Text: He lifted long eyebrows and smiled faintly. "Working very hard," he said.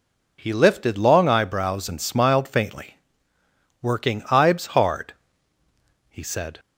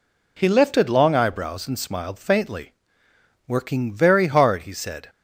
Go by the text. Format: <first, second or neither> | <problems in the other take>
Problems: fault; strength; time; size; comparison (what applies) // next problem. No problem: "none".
second | says "ibes" for "very"; at 4.2 s